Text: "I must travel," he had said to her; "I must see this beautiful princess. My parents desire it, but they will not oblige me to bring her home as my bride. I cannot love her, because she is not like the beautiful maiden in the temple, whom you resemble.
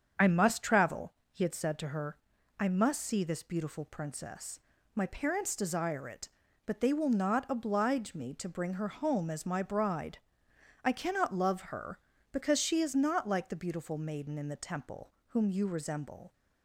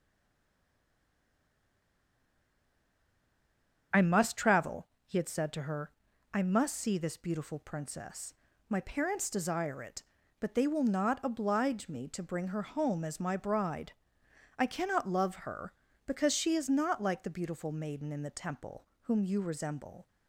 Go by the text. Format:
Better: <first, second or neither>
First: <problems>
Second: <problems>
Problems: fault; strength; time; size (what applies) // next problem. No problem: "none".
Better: first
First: starts louder than the rest; strong; until 1.3 s; 7.5 dB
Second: stays silent before the first word; strong; until 3.9 s; 3.9 s long // starts louder than the rest; strong; until 5.1 s; 7.5 dB